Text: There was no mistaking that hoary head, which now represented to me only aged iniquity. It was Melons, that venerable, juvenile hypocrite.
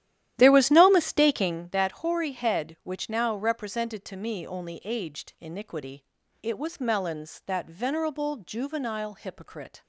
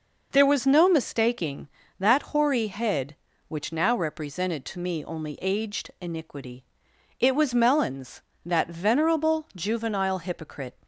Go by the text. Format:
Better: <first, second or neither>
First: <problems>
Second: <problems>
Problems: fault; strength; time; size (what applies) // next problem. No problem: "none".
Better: second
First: starts louder than the rest; strong; until 1.6 s; 12 dB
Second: none